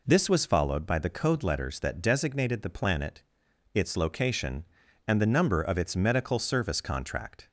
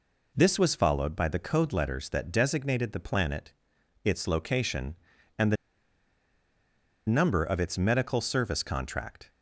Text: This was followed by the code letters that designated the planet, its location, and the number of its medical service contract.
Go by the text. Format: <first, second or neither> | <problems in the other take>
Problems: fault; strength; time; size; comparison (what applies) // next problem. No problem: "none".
first | pauses between "the" and "number"; strong; at 5.5 s; 1.5 s long